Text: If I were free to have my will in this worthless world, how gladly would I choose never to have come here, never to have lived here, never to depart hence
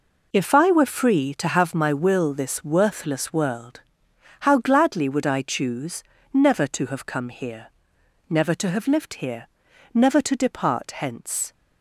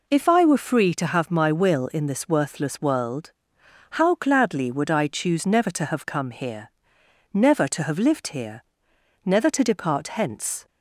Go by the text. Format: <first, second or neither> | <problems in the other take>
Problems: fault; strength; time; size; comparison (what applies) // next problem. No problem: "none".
second | skips "in"; at 2.3 s // pauses between "choose" and "never"; slight; at 6.0 s; 0.28 s long